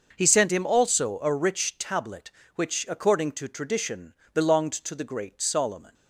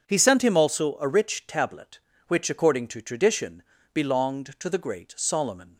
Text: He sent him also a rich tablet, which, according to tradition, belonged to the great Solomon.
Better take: neither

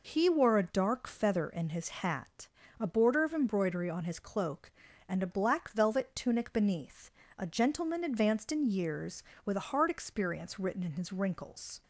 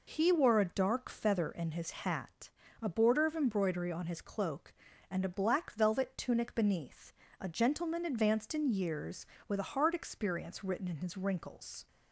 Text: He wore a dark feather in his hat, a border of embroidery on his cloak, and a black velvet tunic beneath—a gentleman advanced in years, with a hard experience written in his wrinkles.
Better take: neither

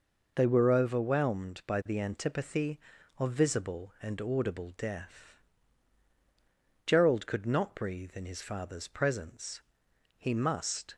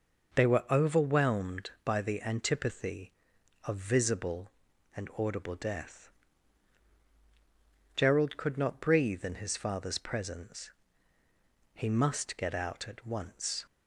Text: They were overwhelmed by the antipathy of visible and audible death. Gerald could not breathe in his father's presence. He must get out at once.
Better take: second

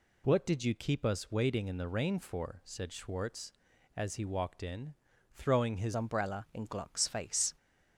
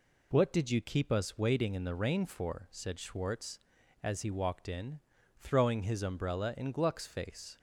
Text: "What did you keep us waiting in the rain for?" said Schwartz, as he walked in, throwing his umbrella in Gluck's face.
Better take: second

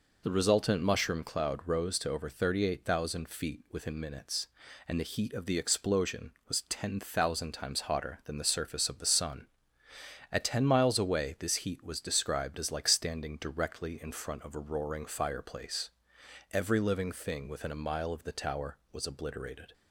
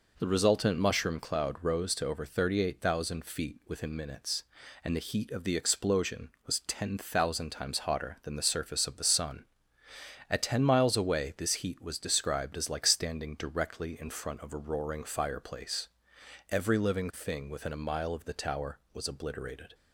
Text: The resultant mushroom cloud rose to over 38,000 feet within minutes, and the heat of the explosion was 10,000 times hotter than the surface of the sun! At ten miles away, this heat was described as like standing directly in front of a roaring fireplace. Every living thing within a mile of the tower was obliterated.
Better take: second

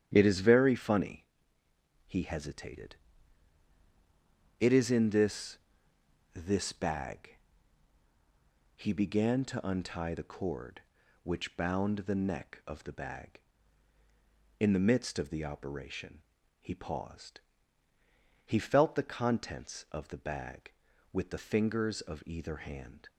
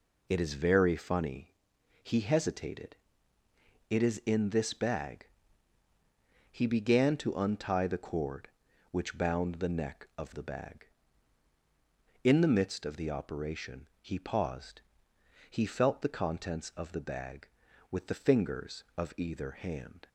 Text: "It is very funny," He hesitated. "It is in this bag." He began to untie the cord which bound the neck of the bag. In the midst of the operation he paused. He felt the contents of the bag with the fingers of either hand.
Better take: second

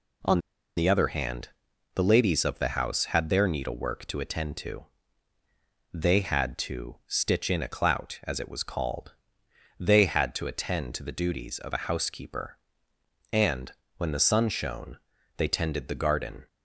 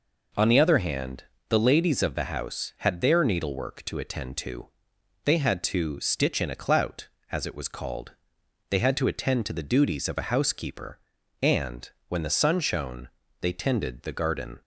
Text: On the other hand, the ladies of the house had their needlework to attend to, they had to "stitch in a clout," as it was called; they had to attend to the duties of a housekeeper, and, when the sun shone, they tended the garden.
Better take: second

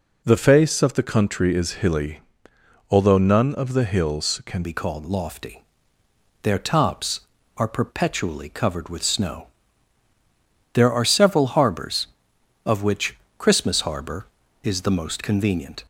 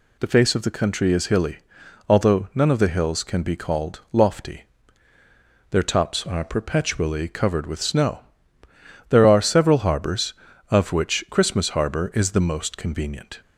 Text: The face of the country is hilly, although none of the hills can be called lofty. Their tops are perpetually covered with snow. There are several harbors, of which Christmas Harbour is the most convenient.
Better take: second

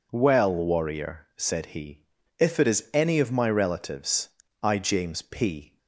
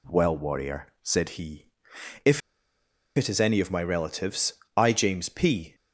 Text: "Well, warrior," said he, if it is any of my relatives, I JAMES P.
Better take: first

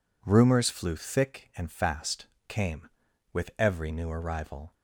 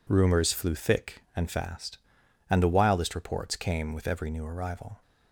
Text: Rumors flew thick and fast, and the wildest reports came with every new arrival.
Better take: second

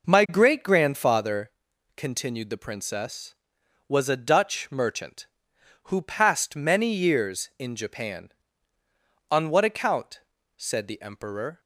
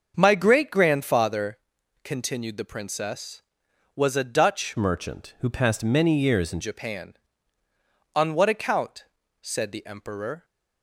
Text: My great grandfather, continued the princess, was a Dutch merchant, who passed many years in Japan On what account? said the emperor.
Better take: first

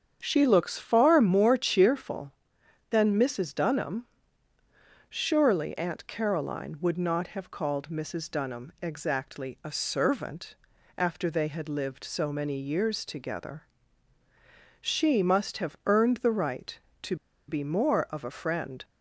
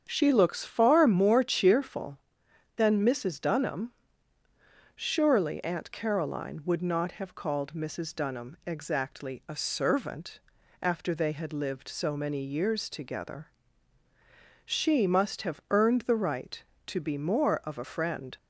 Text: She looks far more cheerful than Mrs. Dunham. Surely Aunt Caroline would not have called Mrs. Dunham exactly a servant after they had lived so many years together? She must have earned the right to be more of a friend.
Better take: second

